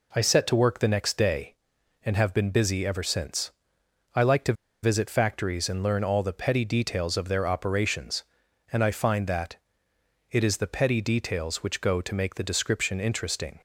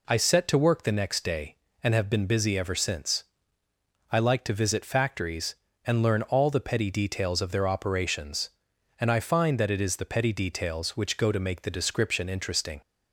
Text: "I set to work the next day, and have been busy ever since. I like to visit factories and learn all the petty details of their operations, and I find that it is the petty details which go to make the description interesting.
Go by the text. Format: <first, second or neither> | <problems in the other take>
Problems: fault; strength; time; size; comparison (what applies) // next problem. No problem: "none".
second | pauses between "to" and "visit"; slight; at 4.5 s; 0.29 s long // pauses between "that" and "it"; noticeable; at 9.5 s; 0.74 s long